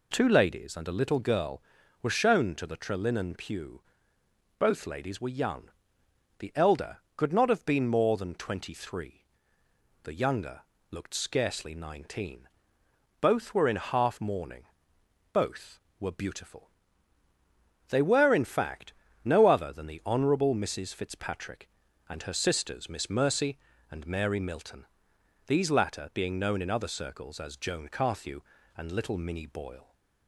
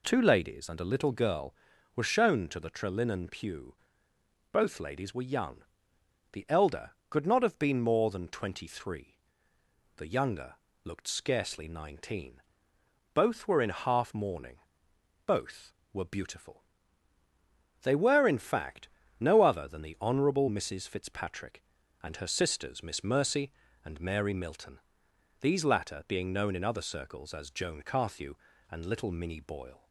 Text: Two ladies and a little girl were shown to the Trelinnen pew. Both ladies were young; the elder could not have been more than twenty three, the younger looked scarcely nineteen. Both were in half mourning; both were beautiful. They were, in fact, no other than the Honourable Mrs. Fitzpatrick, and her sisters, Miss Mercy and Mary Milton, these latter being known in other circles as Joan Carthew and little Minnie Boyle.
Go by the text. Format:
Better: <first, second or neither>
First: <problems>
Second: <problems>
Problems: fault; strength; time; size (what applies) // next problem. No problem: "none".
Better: neither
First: pauses between "younger" and "looked"; slight; at 10.6 s; 0.28 s long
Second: pauses between "younger" and "looked"; slight; at 10.5 s; 0.28 s long